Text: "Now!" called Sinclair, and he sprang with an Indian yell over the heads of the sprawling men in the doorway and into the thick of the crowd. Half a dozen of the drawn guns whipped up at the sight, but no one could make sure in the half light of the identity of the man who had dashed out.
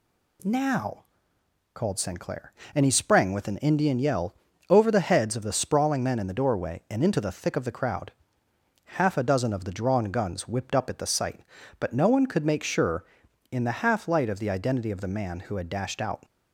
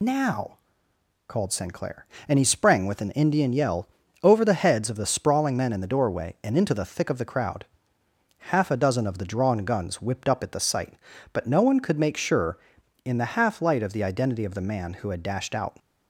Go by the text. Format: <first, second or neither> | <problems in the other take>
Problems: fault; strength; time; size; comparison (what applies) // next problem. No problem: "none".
first | loses the start of "Now"; at 0.0 s; 80 ms // pauses between "yell" and "over"; at 3.8 s; 0.38 s long; also in the first